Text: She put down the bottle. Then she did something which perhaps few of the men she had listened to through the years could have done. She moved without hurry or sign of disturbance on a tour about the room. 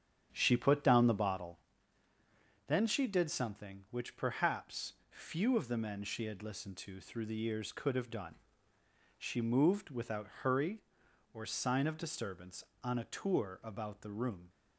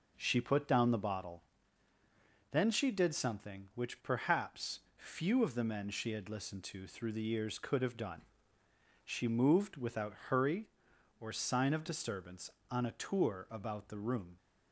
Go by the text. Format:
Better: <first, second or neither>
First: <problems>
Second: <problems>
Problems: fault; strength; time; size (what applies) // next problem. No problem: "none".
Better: second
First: starts louder than the rest; strong; until 1.6 s; 8.5 dB // pauses between "perhaps" and "few"; slight; at 4.9 s; 0.16 s long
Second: pauses between "perhaps" and "few"; slight; at 4.8 s; 0.16 s long